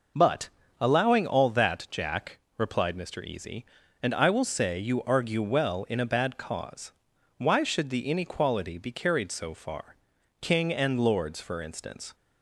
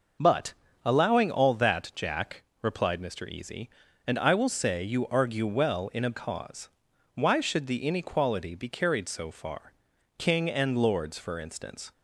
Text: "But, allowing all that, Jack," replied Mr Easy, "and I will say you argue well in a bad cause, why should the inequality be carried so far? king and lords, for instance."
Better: first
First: none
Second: skips "bad"; at 6.1 s

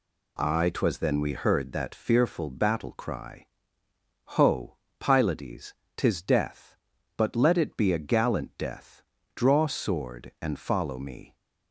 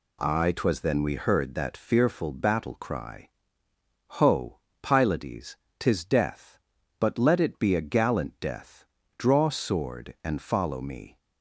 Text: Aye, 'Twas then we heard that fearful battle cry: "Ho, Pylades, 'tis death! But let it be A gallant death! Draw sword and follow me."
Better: neither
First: none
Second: none

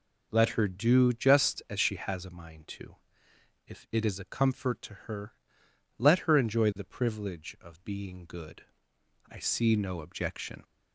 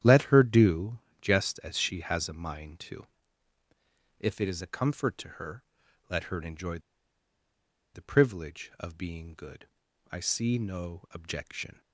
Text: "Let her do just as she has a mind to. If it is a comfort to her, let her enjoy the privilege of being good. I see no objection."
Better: first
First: none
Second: starts louder than the rest; strong; until 1.2 s; 10.5 dB // pauses between "do" and "just"; slight; at 0.9 s; 0.22 s long // pauses between "enjoy" and "the"; at 6.7 s; 1.1 s long

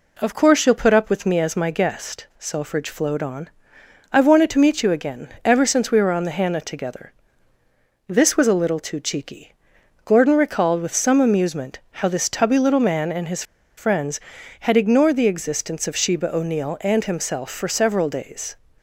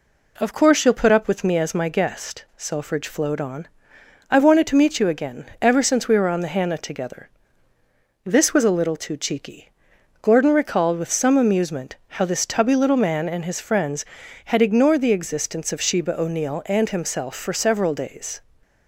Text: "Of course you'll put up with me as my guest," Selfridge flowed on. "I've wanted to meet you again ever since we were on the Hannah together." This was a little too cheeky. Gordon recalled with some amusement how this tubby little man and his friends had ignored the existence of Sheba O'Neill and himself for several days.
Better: second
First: pauses between "again" and "ever"; slight; at 5.2 s; 0.18 s long // pauses between "his" and "friends"; slight; at 13.4 s; 0.33 s long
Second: pauses between "again" and "ever"; slight; at 5.4 s; 0.18 s long

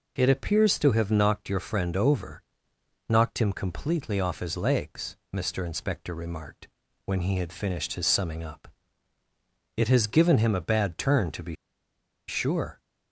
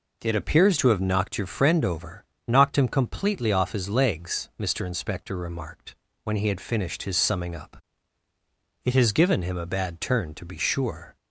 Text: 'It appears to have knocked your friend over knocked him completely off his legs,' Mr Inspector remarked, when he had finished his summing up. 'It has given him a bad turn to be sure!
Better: second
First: pauses between "over" and "knocked"; noticeable; at 2.4 s; 0.66 s long // pauses between "be" and "sure"; noticeable; at 11.5 s; 0.75 s long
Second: pauses between "over" and "knocked"; slight; at 2.2 s; 0.24 s long

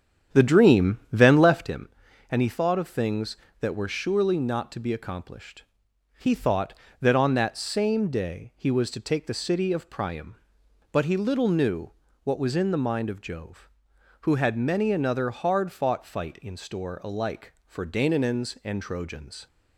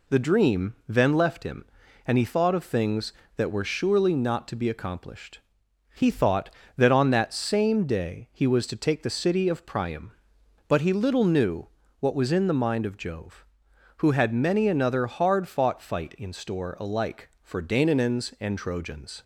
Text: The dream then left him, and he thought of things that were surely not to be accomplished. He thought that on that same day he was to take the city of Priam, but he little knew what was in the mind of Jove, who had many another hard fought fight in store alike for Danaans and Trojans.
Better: second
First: starts louder than the rest; strong; until 1.9 s; 8.5 dB // pauses between "knew" and "what"; slight; at 11.9 s; 0.32 s long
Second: pauses between "knew" and "what"; slight; at 11.6 s; 0.32 s long

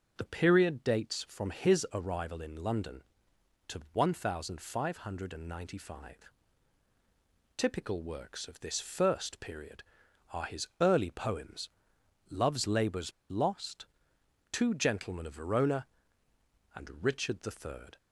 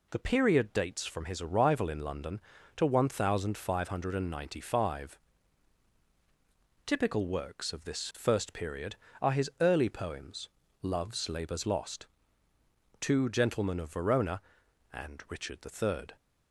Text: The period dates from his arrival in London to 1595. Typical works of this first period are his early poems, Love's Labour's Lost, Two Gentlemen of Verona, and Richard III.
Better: second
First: pauses between "Labour's" and "Lost"; slight; at 13.1 s; 0.19 s long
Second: none

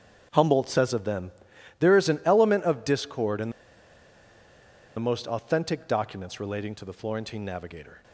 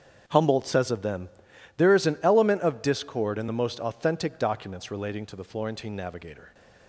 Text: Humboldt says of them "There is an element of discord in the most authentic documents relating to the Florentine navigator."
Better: second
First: starts louder than the rest; strong; until 1.3 s; 7 dB // pauses between "them" and "There"; noticeable; at 1.3 s; 0.48 s long // pauses between "the" and "most"; strong; at 3.5 s; 1.4 s long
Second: starts louder than the rest; strong; until 1.2 s; 7 dB // pauses between "them" and "There"; noticeable; at 1.2 s; 0.48 s long

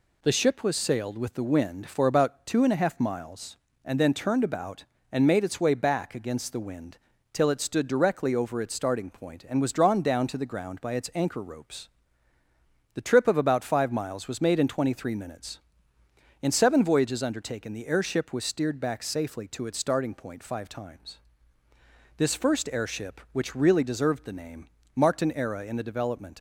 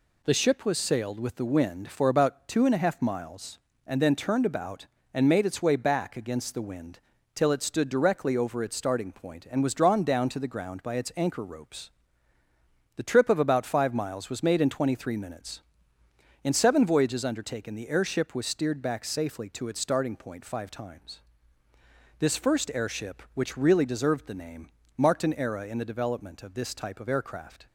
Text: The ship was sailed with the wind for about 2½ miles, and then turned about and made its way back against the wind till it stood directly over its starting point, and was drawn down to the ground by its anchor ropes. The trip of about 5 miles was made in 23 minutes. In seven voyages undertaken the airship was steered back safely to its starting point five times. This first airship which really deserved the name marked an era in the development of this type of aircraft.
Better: second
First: pauses between "wind" and "till"; slight; at 6.9 s; 0.34 s long // pauses between "name" and "marked"; slight; at 24.6 s; 0.28 s long // stops before "of this type of aircraft"; at 26.3 s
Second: pauses between "wind" and "till"; slight; at 7.0 s; 0.34 s long // pauses between "name" and "marked"; slight; at 24.6 s; 0.28 s long

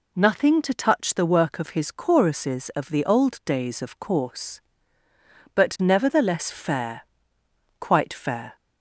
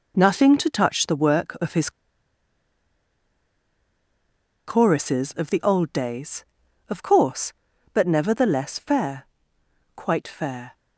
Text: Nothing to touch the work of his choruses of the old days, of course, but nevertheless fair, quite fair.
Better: first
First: none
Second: pauses between "his" and "choruses"; strong; at 1.8 s; 2.7 s long

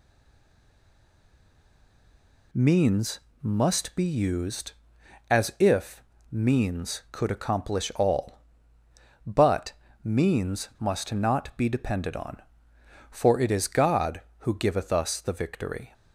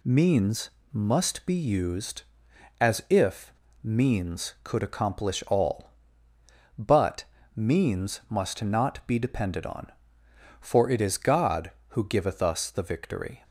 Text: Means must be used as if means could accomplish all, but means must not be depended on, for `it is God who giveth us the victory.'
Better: second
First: stays silent before the first word; until 2.5 s; 2.5 s long // pauses between "Means" and "must"; slight; at 3.1 s; 0.24 s long // pauses between "if" and "means"; slight; at 6.0 s; 0.30 s long // pauses between "but" and "means"; slight; at 9.7 s; 0.30 s long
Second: pauses between "Means" and "must"; slight; at 0.6 s; 0.24 s long // pauses between "if" and "means"; slight; at 3.5 s; 0.31 s long // pauses between "but" and "means"; slight; at 7.2 s; 0.30 s long

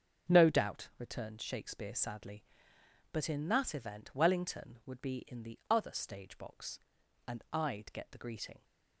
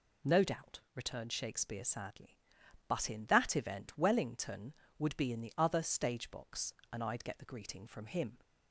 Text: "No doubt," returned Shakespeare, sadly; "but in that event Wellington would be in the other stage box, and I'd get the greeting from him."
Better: second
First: starts louder than the rest; until 1.3 s; 6.5 dB // stops before "from him"; at 8.6 s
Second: none

